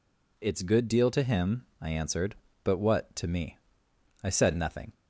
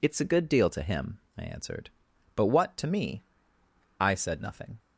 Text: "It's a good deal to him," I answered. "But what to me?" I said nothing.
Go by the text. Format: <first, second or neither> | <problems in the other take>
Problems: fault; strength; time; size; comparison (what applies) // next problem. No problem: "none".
second | skips "a"; at 0.6 s